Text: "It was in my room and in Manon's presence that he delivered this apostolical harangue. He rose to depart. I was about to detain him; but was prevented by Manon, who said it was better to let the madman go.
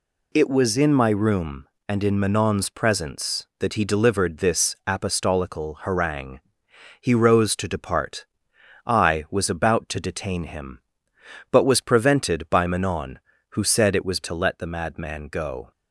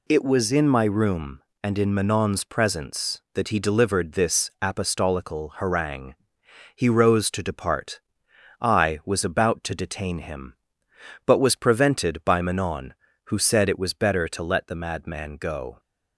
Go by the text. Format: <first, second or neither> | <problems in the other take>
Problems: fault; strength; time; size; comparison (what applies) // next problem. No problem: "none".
second | skips "better"; at 14.2 s